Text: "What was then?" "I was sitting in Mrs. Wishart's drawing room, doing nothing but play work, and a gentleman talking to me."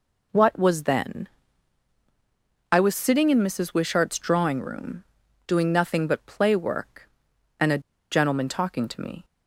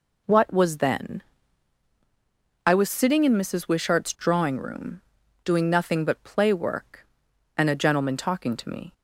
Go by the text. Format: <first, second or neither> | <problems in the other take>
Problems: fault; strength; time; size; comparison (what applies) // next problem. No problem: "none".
second | pauses between "a" and "gentleman"; slight; at 7.7 s; 0.32 s long